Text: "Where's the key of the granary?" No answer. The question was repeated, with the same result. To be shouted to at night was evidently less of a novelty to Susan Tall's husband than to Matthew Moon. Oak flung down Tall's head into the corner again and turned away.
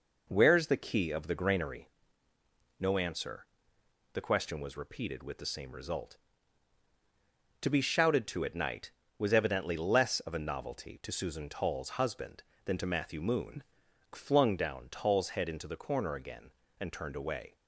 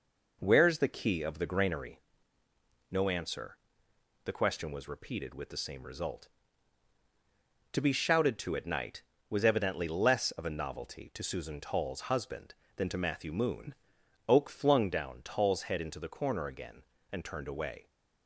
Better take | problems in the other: second | skips "Oak"; at 13.8 s

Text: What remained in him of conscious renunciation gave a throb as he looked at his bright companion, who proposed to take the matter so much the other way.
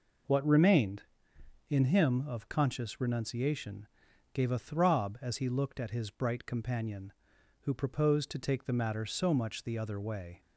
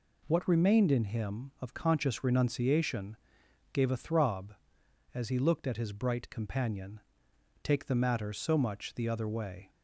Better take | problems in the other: first | pauses between "renunciation" and "gave"; noticeable; at 3.1 s; 0.56 s long; noticeable in the first // skips "who proposed to"; at 7.3 s

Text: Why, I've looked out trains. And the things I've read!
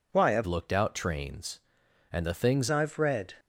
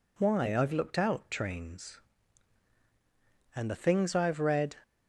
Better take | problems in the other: second | changes voice from "looked" to "things"; from 0.4 to 2.6 s; 2.2 s long

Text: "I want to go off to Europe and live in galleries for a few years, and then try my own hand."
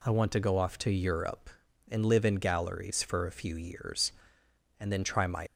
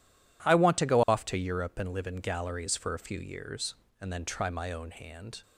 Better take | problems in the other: second | stops before "own hand"; at 5.4 s

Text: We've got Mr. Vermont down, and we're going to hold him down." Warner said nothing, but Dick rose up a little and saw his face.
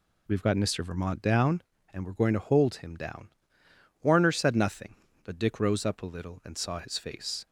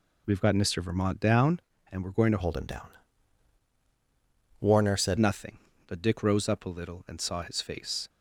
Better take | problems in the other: first | changes voice from "hold" to "said"; from 2.4 to 5.1 s; 2.7 s long

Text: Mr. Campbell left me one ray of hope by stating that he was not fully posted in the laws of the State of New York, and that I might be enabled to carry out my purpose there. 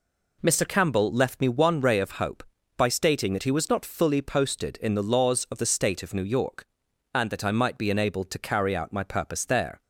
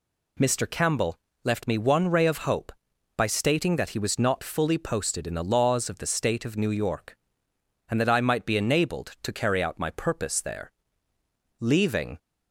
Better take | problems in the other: first | pauses between "Campbell" and "left"; slight; at 1.1 s; 0.28 s long // goes on to say "Leaving"; from 11.5 s on; 0.58 s long

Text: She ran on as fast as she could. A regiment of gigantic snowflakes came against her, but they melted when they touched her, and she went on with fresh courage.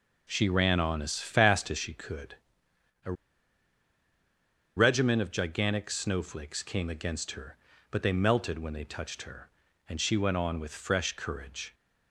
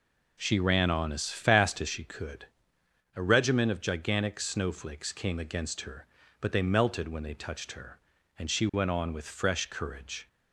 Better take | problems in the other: second | pauses between "A" and "regiment"; strong; at 3.1 s; 1.6 s long

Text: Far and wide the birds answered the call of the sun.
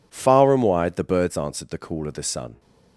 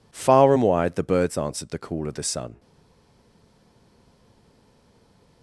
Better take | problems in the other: first | stays silent after the last word; strong; from 2.5 s on; 2.9 s long

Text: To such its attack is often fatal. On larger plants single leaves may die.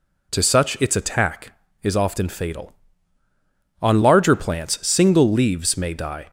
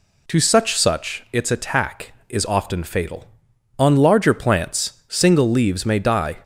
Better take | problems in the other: first | says "such" twice; at 0.7 s

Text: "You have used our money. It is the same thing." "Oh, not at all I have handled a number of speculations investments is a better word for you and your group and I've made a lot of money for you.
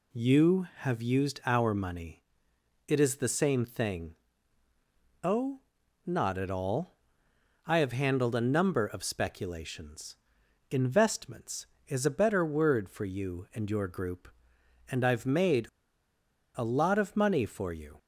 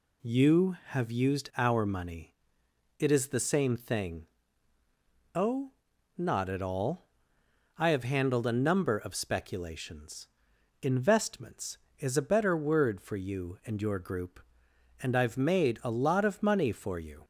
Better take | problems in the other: second | pauses between "all" and "I"; noticeable; at 6.9 s; 0.68 s long; noticeable in the second // pauses between "speculations" and "investments"; noticeable; at 10.1 s; 0.52 s long; noticeable in the second // pauses between "made" and "a"; noticeable; at 15.6 s; 0.87 s long

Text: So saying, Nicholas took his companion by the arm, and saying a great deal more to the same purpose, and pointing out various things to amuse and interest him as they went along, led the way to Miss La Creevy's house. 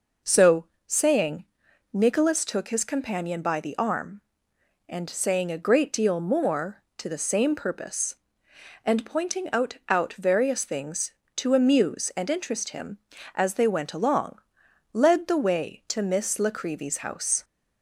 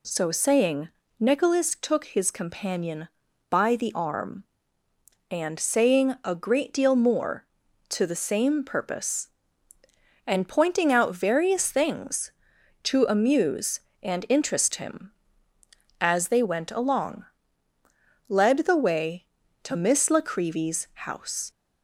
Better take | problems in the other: second | pauses between "So" and "saying"; slight; at 0.6 s; 0.20 s long // says "out" twice; at 9.8 s

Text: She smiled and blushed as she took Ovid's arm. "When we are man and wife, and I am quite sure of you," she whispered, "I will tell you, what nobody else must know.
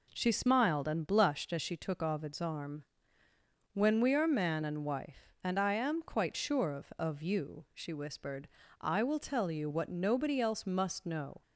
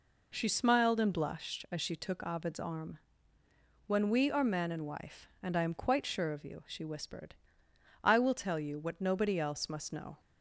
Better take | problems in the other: second | says "of" twice; at 6.9 s

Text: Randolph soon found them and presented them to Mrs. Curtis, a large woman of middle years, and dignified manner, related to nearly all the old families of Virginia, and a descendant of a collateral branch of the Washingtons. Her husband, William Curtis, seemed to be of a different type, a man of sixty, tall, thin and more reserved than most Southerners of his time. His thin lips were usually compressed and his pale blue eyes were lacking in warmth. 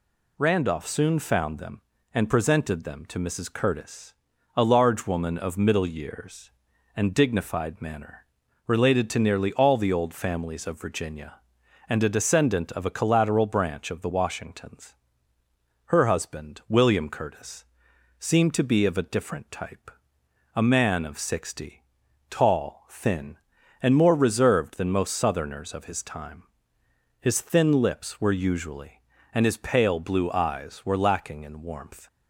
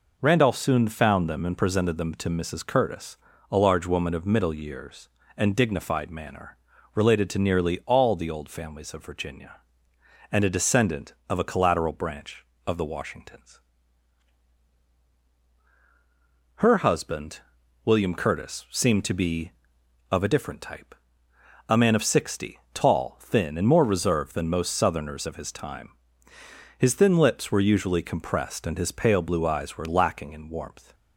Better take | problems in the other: second | skips "compressed"; at 29.1 s

